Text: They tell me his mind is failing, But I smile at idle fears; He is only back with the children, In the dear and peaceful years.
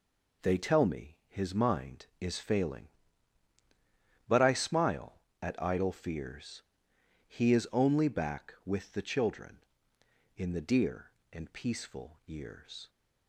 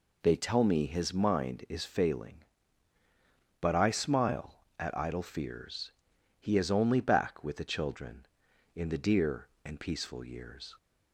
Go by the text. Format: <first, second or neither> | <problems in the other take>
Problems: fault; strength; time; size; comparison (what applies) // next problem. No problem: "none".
neither | none